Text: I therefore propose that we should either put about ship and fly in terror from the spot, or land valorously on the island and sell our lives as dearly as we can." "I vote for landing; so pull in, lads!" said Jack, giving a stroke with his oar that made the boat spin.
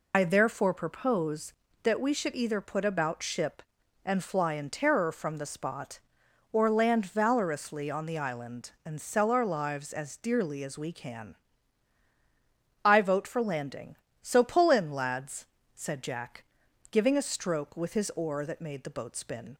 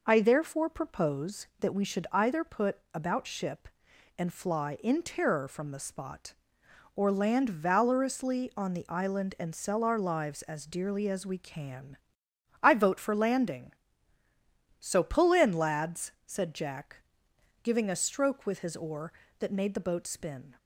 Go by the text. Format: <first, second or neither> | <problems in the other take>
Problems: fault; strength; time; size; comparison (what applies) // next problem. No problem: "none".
second | loses the start of "I"; at 0.1 s; 60 ms